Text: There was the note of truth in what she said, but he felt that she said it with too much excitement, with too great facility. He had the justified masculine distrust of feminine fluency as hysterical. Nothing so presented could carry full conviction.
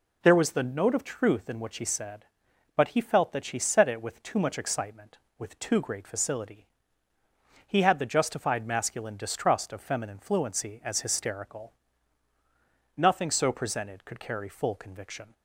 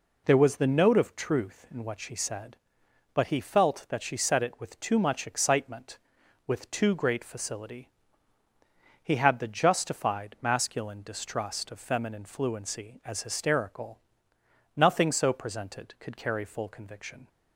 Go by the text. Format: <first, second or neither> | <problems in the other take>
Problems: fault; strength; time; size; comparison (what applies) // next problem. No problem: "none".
neither | none